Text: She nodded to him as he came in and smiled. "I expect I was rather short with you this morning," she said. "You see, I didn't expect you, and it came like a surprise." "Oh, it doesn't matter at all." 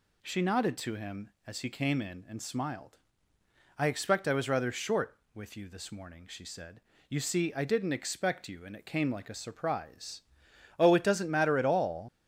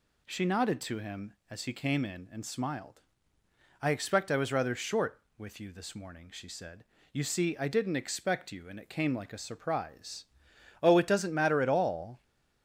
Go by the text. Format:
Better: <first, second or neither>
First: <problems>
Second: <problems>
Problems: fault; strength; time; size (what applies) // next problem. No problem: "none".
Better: second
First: leaves "all" unfinished; at 12.0 s; 105 ms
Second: none